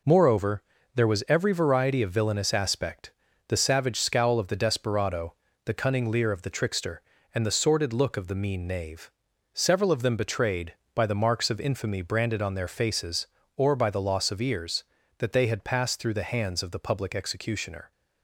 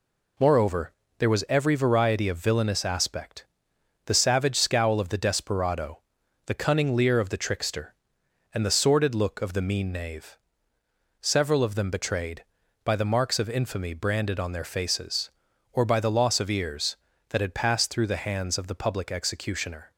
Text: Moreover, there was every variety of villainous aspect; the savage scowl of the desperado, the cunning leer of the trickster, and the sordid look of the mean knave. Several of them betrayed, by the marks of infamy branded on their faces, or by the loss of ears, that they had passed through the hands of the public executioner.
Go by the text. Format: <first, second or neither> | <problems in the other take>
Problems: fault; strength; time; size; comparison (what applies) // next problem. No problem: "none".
first | skips "they"; at 17.4 s